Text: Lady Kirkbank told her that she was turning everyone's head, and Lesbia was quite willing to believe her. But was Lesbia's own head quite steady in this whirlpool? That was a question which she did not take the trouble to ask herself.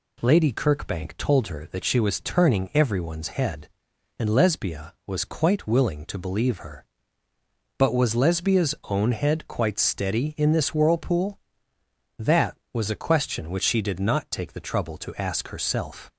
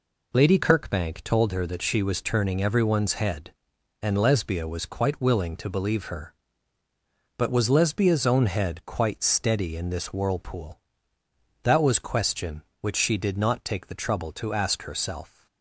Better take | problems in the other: first | skips "a"; at 11.9 s

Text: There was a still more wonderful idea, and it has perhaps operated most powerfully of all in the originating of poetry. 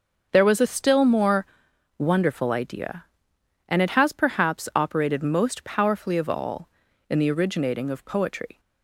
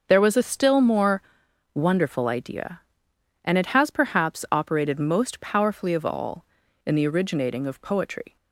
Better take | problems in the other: neither | starts louder than the rest; the same in both // pauses between "more" and "wonderful"; noticeable; the same in both

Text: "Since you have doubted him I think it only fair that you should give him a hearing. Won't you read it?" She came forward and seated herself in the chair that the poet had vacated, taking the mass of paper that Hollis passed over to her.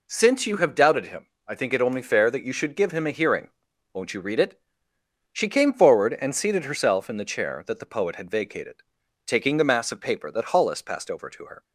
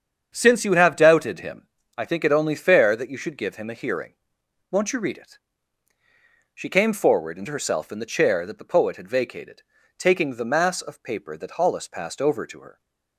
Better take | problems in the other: first | starts louder than the rest; strong; until 1.3 s; 7.5 dB // pauses between "him" and "I"; slight; at 1.6 s; 0.28 s long; slight in the first // skips "seated"; at 7.4 s

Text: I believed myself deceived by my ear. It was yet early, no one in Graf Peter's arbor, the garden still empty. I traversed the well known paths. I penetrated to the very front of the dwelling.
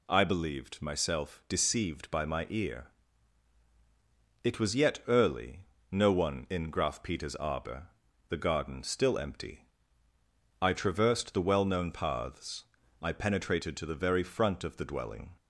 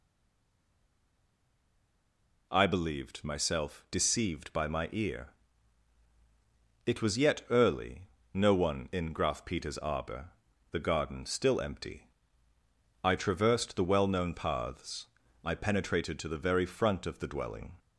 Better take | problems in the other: first | stays silent before the first word; until 2.5 s; 2.5 s long

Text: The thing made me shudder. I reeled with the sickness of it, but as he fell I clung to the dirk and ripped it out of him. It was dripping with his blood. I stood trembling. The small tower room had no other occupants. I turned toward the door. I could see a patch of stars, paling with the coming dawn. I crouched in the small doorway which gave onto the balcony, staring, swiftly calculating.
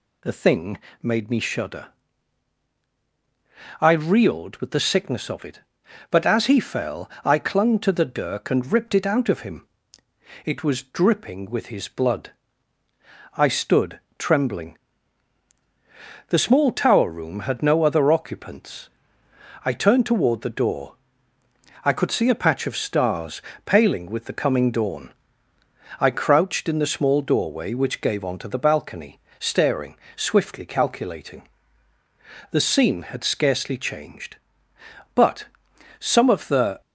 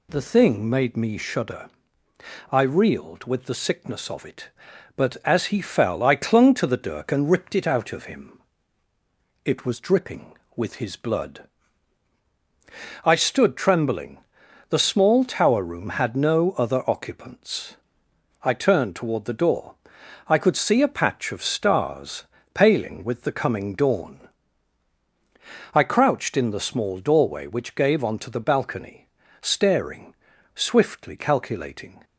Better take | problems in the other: second | pauses between "thing" and "made"; slight; at 0.7 s; 0.24 s long // pauses between "fell" and "I"; slight; at 7.0 s; 0.16 s long // pauses between "stood" and "trembling"; slight; at 14.0 s; 0.18 s long // goes on to say "The scene had scarcely changed But some of the"; strong; from 32.5 s on; 4.3 s long

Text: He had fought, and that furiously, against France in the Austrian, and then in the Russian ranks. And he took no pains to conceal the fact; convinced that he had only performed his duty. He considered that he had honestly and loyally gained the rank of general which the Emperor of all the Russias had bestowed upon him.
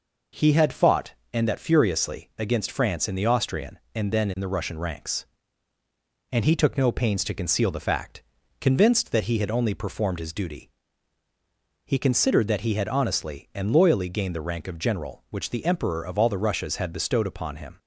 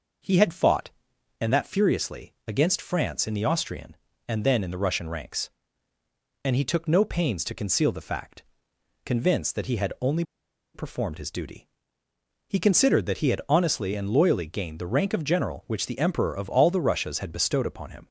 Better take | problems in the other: first | pauses between "only" and "performed"; noticeable; at 10.2 s; 0.51 s long

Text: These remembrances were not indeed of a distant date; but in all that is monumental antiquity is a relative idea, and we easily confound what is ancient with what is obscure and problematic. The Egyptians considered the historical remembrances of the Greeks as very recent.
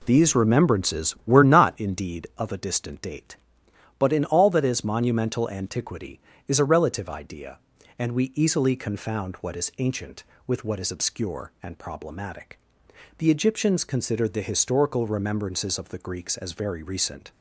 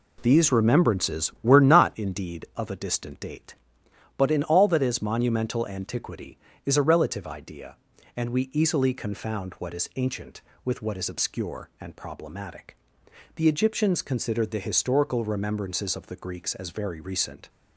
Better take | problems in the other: neither | none

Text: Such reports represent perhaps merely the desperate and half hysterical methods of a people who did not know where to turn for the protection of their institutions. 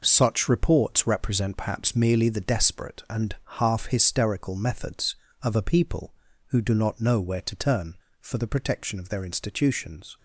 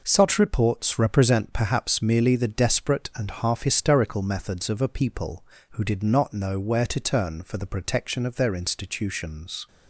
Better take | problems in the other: second | pauses between "and" and "half"; slight; at 3.3 s; 0.18 s long // says "do" for "did"; at 6.5 s

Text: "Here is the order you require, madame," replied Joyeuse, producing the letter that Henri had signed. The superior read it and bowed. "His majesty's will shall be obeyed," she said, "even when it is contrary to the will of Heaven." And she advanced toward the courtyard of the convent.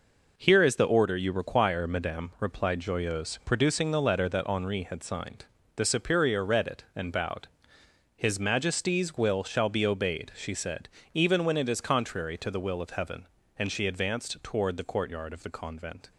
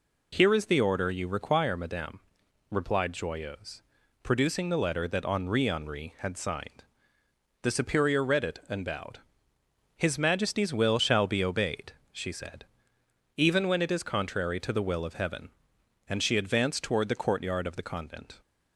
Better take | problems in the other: first | says "Henri" twice; at 5.6 s

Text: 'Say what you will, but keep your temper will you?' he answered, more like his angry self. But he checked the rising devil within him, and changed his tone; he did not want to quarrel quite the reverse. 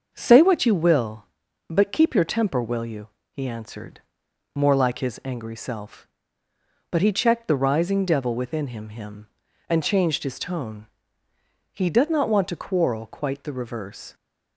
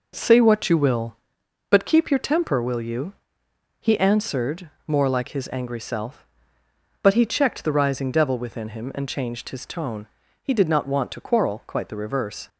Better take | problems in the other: second | starts louder than the rest; until 1.1 s; 6.5 dB // says "him" twice; at 8.8 s

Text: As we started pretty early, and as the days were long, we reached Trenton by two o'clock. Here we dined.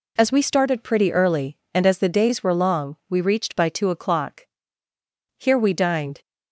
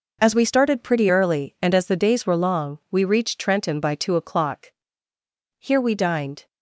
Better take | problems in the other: second | skips "Trenton"; at 3.5 s

